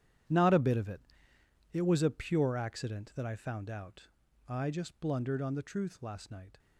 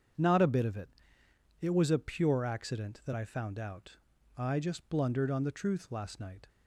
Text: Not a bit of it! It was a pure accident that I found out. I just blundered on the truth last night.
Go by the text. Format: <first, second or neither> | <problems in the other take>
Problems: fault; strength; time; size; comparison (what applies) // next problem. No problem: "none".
second | gets quieter; strong; throughout; 15.5 dB // starts louder than the rest; strong; until 2.0 s; 10 dB; strong in the second